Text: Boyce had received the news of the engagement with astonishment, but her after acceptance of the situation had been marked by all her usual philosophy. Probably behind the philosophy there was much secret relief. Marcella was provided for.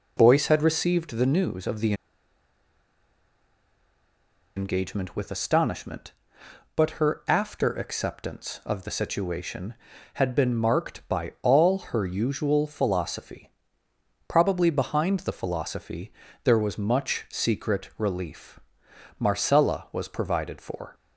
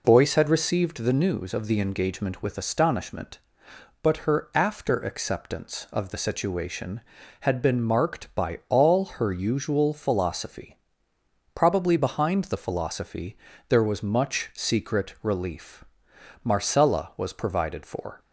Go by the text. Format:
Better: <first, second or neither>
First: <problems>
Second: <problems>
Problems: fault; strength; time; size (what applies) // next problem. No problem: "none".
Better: second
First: pauses between "the" and "engagement"; strong; at 1.9 s; 2.6 s long // pauses between "philosophy" and "there"; slight; at 16.1 s; 0.32 s long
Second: pauses between "philosophy" and "there"; slight; at 13.3 s; 0.32 s long